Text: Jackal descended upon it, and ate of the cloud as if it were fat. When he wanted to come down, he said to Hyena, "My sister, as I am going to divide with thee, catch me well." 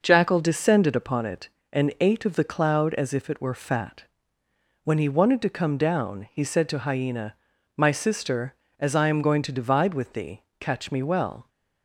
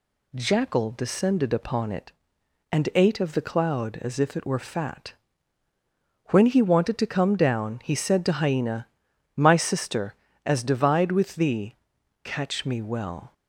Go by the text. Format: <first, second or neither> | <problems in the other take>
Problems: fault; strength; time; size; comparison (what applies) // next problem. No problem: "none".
first | skips "I am going to"; at 10.6 s